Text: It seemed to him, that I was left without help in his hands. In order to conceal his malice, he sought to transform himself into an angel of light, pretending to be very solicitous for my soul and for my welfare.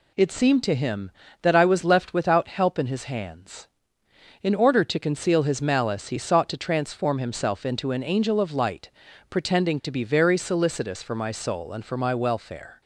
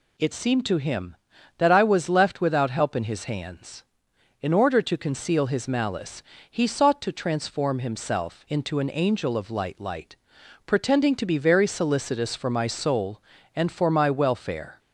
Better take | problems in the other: first | says "light" twice; at 9.8 s

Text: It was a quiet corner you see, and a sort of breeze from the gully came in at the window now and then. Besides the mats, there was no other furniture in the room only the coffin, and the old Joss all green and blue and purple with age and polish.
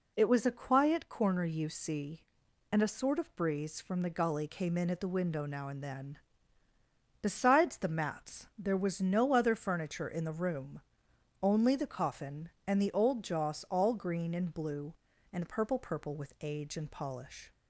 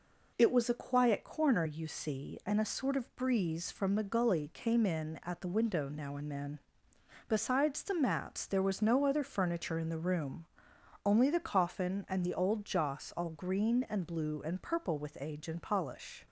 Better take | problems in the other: second | pauses between "room" and "only"; noticeable; at 10.8 s; 0.60 s long; noticeable in the second // says "purple" twice; at 15.7 s

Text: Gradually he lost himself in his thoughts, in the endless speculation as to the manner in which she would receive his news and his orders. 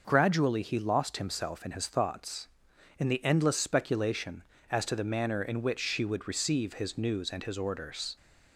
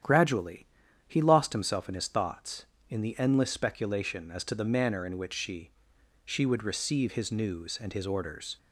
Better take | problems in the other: first | starts louder than the rest; strong; until 1.4 s; 9.5 dB // pauses between "Gradually" and "he"; at 0.6 s; 0.40 s long // says "she" twice; at 6.2 s

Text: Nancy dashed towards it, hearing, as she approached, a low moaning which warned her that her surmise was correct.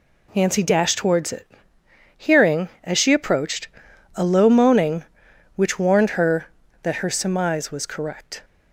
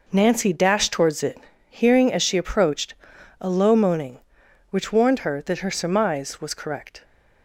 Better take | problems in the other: neither | none

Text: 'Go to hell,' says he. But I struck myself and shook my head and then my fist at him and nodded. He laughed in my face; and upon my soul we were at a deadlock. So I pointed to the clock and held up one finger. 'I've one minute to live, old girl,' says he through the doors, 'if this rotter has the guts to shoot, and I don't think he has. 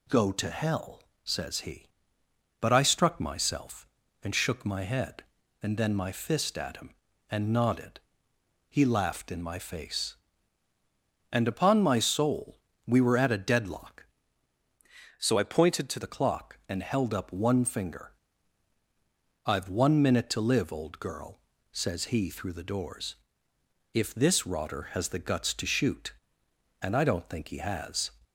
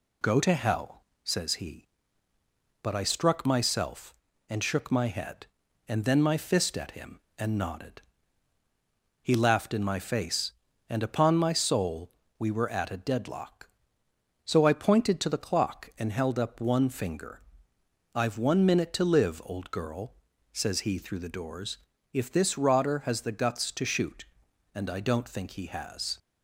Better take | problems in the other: second | pauses between "soul" and "we"; slight; at 12.5 s; 0.28 s long; slight in the second // changes voice from "So" to "to"; from 15.1 to 15.9 s; 0.8 s long

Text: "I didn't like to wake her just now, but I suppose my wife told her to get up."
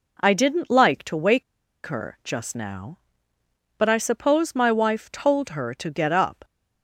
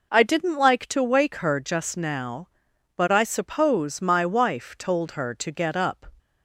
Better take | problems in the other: second | pauses between "wake" and "her"; at 1.4 s; 0.43 s long

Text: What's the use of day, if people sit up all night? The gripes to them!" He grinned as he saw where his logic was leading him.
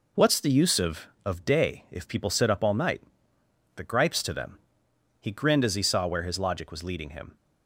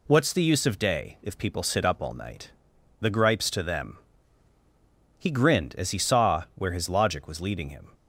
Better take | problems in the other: second | says "of" twice; at 1.2 s

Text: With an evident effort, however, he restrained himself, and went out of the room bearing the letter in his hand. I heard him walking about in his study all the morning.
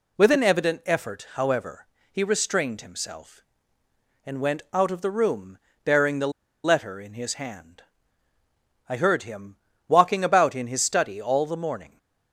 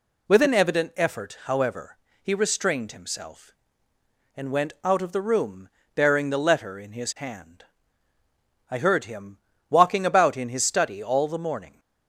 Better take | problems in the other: second | pauses between "room" and "bearing"; slight; at 5.5 s; 0.26 s long; slight in the second // pauses between "the" and "letter"; slight; at 6.3 s; 0.33 s long // pauses between "him" and "walking"; slight; at 9.5 s; 0.32 s long; slight in the second

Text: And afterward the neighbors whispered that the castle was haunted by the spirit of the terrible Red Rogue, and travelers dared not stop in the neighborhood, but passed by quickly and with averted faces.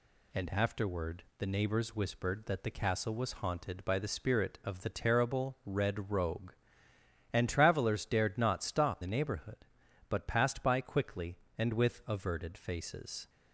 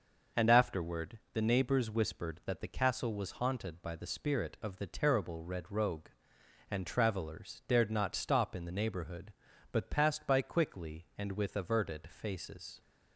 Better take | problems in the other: second | pauses between "afterward" and "the"; slight; at 1.2 s; 0.16 s long // skips "in"; at 9.0 s

